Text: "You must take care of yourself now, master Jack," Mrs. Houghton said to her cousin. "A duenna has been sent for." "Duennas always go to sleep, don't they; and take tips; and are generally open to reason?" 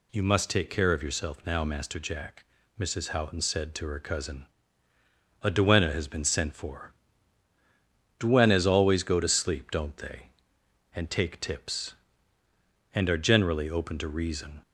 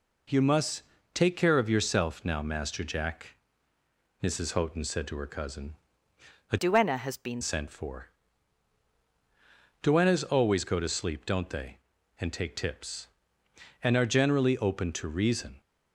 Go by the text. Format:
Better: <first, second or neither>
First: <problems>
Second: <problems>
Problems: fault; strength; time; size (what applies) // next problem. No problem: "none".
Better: first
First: none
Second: pauses between "must" and "take"; slight; at 0.8 s; 0.32 s long // changes voice from "duenna" to "been"; from 6.5 to 7.4 s; 0.9 s long